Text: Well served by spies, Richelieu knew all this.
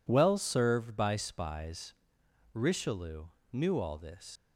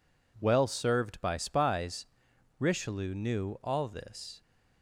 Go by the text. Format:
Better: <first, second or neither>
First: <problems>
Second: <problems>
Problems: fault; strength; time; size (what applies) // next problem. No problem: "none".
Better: second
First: pauses between "Richelieu" and "knew"; slight; at 3.2 s; 0.26 s long // leaves "this" unfinished; at 4.3 s; 100 ms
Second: none